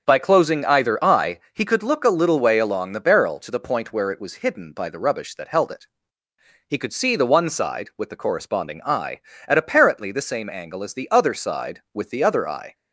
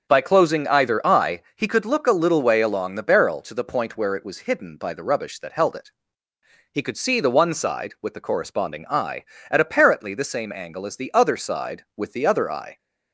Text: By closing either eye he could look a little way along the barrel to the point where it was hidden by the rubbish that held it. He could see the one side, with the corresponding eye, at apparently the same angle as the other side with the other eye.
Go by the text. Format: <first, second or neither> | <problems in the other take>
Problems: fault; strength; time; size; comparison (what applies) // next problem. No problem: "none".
neither | starts louder than the rest; the same in both